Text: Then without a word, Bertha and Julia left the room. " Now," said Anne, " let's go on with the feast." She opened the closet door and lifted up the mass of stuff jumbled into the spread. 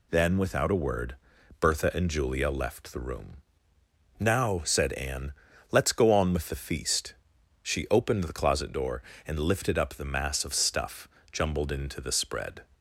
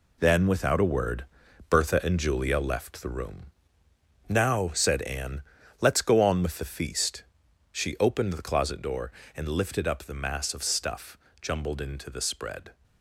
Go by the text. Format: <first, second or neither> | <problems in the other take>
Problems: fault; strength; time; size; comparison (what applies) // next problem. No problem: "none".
first | gets quieter; noticeable; throughout; 5 dB // pauses between "stuff" and "jumbled"; slight; at 11.1 s; 0.24 s long; slight in the first